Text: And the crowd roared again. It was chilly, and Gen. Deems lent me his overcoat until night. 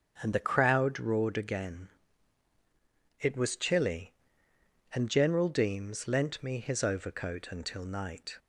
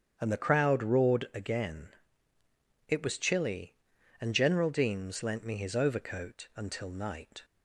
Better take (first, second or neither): neither